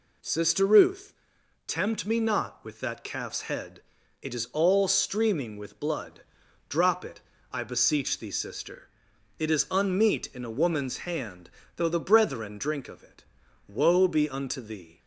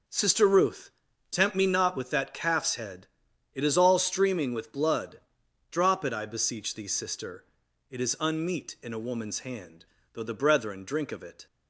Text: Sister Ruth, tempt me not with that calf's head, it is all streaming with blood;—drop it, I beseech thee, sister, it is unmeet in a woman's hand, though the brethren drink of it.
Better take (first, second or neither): second